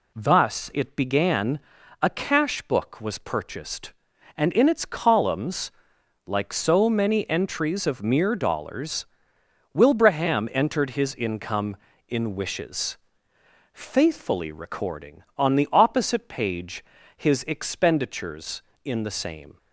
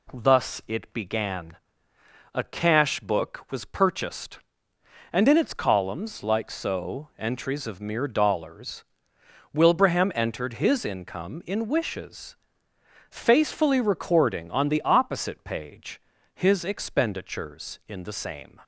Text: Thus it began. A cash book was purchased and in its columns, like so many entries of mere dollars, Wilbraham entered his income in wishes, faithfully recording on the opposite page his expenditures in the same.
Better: first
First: pauses between "page" and "his"; slight; at 16.8 s; 0.32 s long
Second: skips "many"; at 7.1 s // pauses between "page" and "his"; slight; at 15.9 s; 0.36 s long

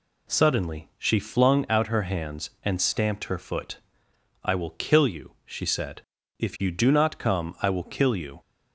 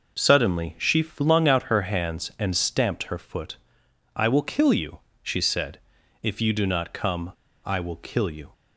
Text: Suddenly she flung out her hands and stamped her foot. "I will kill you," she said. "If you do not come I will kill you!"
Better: first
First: none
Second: pauses between "come" and "I"; slight; at 7.3 s; 0.33 s long

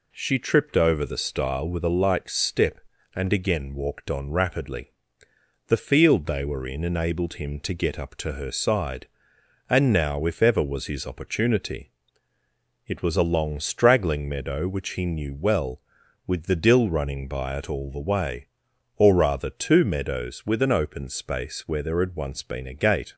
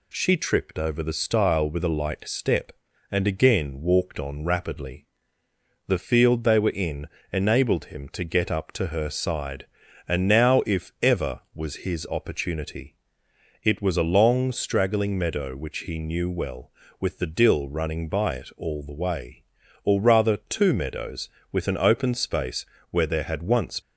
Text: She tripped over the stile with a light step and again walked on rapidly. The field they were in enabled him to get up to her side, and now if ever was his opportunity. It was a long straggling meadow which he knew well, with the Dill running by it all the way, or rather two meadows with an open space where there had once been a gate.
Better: first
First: none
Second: pauses between "in" and "enabled"; slight; at 7.0 s; 0.26 s long // pauses between "space" and "where"; slight; at 22.6 s; 0.26 s long // stops before "been a gate"; at 23.8 s

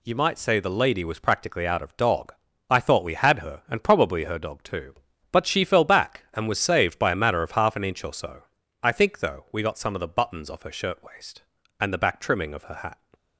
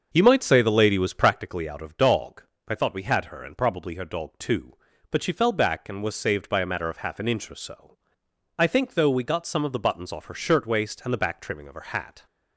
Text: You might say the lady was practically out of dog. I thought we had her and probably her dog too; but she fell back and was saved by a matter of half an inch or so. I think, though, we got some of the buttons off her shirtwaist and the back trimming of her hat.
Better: first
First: none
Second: starts louder than the rest; until 1.5 s; 6.5 dB

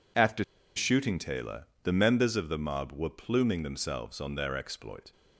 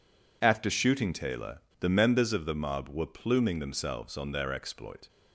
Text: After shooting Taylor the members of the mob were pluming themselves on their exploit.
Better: second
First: pauses between "After" and "shooting"; slight; at 0.4 s; 0.34 s long // pauses between "Taylor" and "the"; slight; at 1.6 s; 0.18 s long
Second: pauses between "Taylor" and "the"; slight; at 1.5 s; 0.20 s long

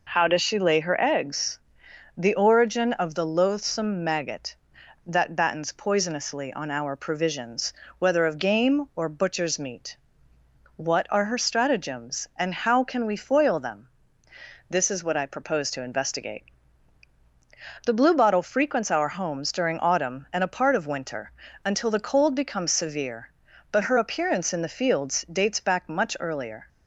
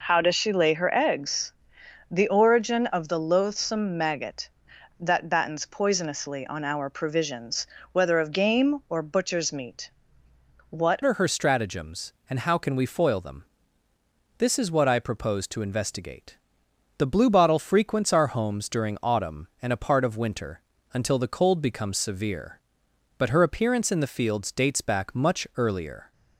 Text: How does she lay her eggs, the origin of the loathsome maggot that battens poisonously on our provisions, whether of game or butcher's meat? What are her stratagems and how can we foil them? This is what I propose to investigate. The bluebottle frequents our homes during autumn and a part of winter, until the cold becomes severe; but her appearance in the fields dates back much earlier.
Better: first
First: none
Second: changes voice at "are"; from 11.0 s on; 15.1 s long

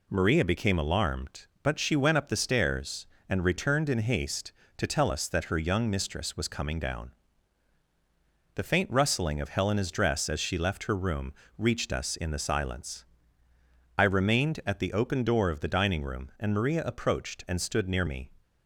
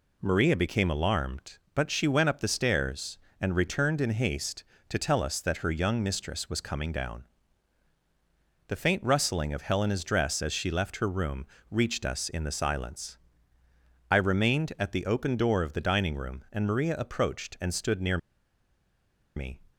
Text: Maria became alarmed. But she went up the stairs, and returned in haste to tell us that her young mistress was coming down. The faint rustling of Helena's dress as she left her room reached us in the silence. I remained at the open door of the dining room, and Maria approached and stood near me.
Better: first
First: pauses between "room" and "reached"; slight; at 11.3 s; 0.24 s long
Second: pauses between "room" and "reached"; slight; at 11.4 s; 0.24 s long // pauses between "near" and "me"; at 18.1 s; 1.1 s long

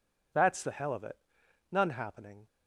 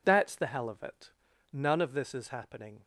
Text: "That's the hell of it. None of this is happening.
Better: second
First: skips "of this is"; at 1.9 s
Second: none

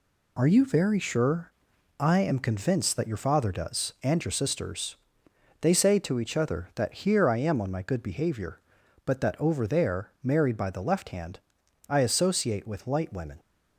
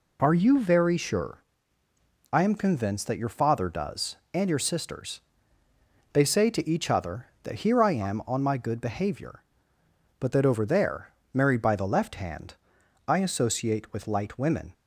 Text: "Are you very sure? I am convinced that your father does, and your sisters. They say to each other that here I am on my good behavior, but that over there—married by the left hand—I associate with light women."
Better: neither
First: none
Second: none

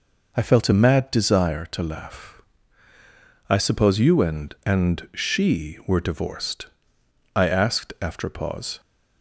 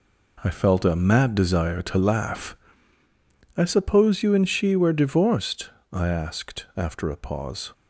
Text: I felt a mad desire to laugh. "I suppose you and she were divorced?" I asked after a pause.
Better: second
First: says "and" twice; at 4.6 s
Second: none

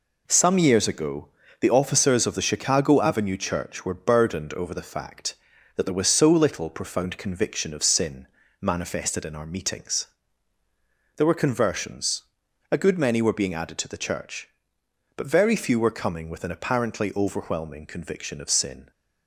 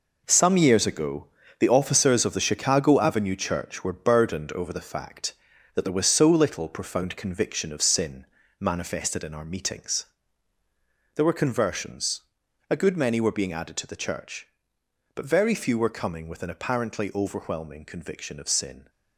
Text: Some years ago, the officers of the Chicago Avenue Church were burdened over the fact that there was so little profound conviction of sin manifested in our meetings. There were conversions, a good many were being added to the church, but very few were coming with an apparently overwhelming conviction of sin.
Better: first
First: pauses between "sin" and "manifested"; slight; at 8.2 s; 0.34 s long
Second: gets quieter; strong; throughout; 9.5 dB // pauses between "sin" and "manifested"; slight; at 8.2 s; 0.34 s long

